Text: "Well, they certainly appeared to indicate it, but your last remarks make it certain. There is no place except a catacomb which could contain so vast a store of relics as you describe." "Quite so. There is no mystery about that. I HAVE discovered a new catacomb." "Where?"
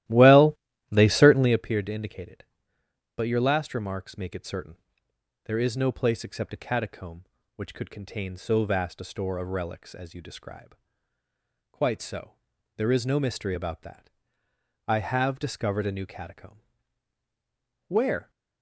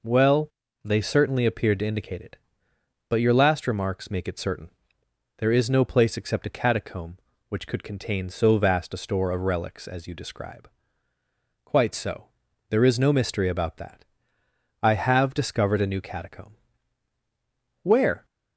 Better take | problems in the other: second | starts louder than the rest; strong; until 1.7 s; 14.5 dB

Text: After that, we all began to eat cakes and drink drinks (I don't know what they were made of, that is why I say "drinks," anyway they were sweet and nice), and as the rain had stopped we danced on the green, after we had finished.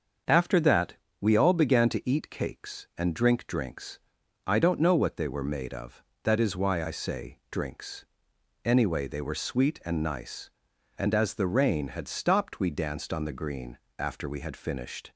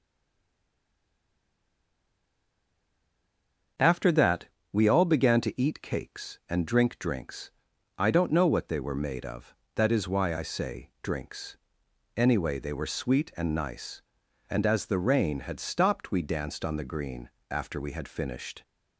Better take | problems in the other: first | stays silent before the first word; strong; until 3.7 s; 3.7 s long // starts louder than the rest; until 5.0 s; 7 dB; also in the first

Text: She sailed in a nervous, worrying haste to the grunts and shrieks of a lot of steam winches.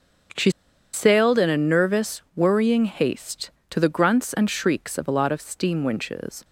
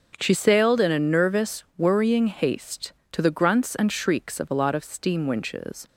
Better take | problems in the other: second | starts louder than the rest; strong; until 1.8 s; 7.5 dB; strong in the second // pauses between "She" and "sailed"; at 0.5 s; 0.42 s long

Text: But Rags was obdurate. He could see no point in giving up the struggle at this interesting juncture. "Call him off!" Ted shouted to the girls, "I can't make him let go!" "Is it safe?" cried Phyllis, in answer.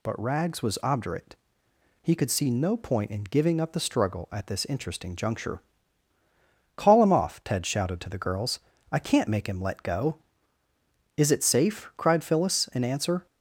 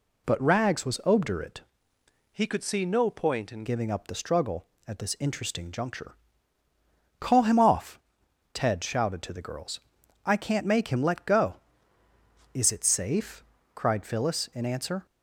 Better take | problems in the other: first | changes voice from "He" to "in"; from 2.3 to 3.6 s; 1.3 s long

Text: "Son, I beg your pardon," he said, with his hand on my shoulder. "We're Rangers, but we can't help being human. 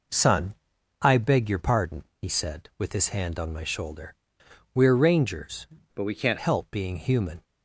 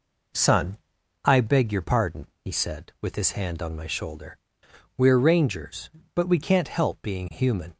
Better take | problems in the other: second | changes voice from "but" to "can't"; from 5.9 to 6.3 s; 0.4 s long

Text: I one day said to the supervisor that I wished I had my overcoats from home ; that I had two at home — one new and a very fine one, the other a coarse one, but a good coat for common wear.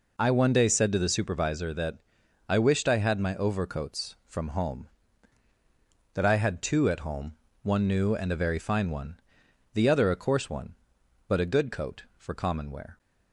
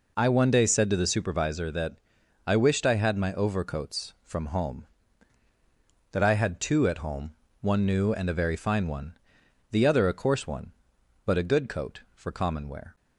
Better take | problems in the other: neither | pauses between "that" and "I"; noticeable; the same in both

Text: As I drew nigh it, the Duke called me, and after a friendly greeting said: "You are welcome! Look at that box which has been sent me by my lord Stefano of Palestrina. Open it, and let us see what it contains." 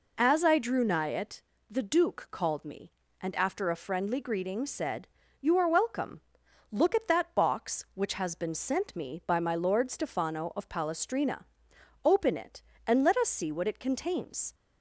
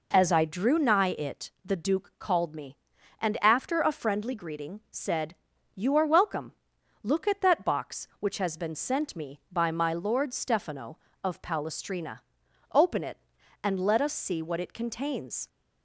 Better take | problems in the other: neither | none

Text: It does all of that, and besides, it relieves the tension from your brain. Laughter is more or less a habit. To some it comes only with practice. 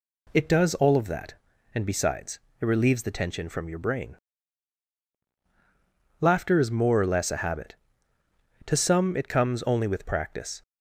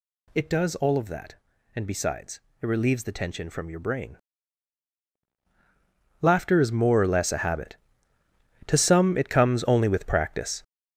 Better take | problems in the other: first | gets louder; strong; throughout; 7.5 dB

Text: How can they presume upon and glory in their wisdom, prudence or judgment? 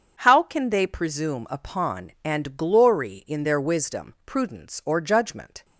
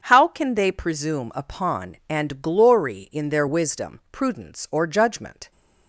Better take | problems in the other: neither | starts louder than the rest; strong; the same in both

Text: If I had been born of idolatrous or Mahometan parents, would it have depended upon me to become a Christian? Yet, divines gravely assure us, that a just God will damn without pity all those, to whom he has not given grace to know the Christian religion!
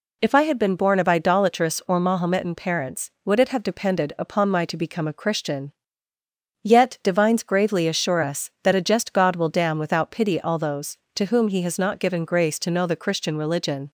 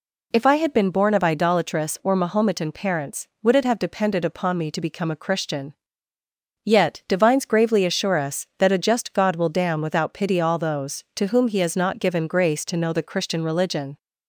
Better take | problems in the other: second | says "my" for "me"; at 4.4 s

